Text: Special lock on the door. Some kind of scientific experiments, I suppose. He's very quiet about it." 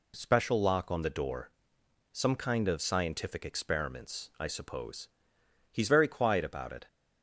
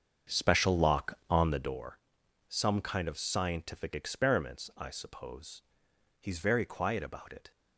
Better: first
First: none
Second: starts louder than the rest; strong; until 1.8 s; 7 dB

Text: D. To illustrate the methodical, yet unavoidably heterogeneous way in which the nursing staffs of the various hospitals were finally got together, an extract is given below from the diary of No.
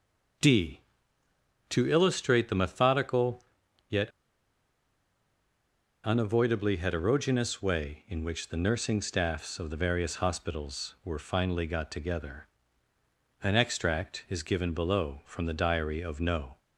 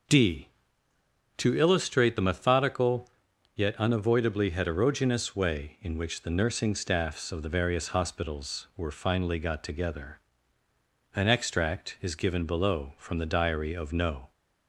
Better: second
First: pauses between "yet" and "unavoidably"; strong; at 4.0 s; 1.9 s long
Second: none

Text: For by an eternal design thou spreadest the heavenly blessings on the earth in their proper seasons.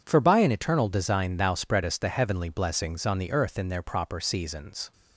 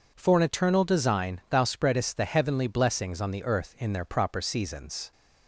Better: first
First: none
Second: skips "by"; at 0.3 s

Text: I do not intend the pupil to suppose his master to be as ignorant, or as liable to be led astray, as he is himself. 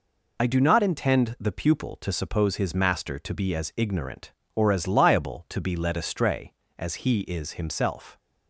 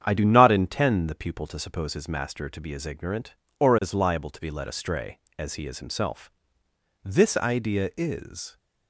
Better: first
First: none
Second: starts louder than the rest; strong; until 1.0 s; 8.5 dB // goes on to say "This idea is"; from 7.0 s on; 1.5 s long

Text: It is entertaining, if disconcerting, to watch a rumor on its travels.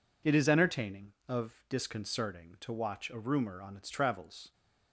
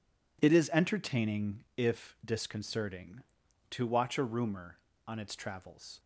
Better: second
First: says "of" for "if"; at 1.2 s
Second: none

